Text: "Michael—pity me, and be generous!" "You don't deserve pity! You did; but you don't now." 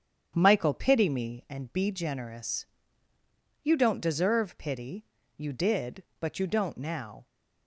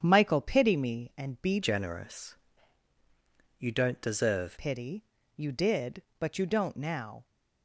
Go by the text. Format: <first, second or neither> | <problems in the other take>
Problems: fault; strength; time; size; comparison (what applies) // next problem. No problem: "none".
first | starts louder than the rest; strong; until 1.0 s; 8.5 dB; strong in the first // changes voice from "generous" to "deserve"; from 1.6 to 4.5 s; 2.9 s long